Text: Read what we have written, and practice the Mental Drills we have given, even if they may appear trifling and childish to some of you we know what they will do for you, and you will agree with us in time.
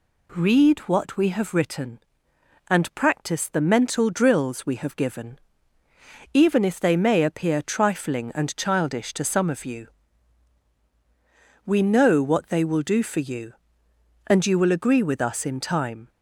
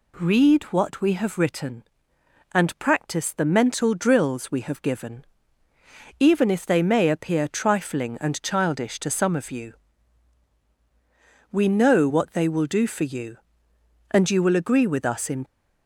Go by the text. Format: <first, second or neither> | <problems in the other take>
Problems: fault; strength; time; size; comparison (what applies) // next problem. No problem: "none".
first | pauses between "you" and "we"; strong; at 9.7 s; 1.7 s long; strong in the first // stops before "time"; at 15.4 s